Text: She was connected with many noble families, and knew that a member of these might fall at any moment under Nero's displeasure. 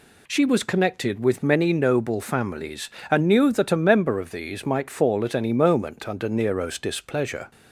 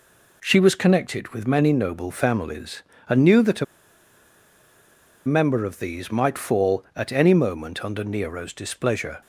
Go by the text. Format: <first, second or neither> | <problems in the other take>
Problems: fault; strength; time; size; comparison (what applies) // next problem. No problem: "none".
first | pauses between "a" and "member"; strong; at 3.6 s; 1.6 s long